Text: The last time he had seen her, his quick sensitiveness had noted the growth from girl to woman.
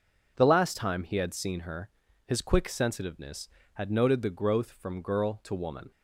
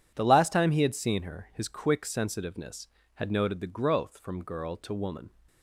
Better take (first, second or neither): neither